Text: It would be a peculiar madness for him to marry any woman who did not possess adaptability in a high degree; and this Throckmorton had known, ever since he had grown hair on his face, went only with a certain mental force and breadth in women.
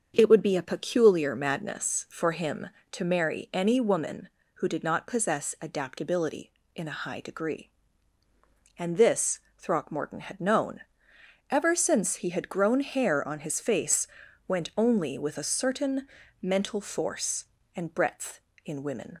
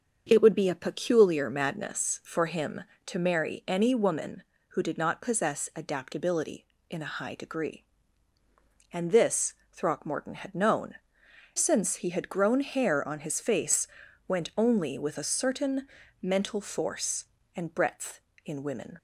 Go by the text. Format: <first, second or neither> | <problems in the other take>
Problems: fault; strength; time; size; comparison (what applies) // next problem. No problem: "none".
first | starts louder than the rest; until 1.2 s; 7 dB; also in the first // pauses between "this" and "Throckmorton"; slight; at 9.5 s; 0.18 s long; slight in the first // skips "ever"; at 11.2 s // pauses between "certain" and "mental"; slight; at 15.8 s; 0.36 s long; slight in the first